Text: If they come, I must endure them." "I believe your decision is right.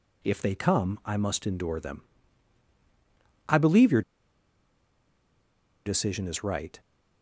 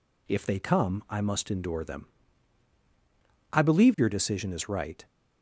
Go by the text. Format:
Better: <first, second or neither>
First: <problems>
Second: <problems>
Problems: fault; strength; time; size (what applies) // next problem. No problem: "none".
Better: second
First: pauses between "your" and "decision"; strong; at 4.0 s; 1.8 s long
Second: none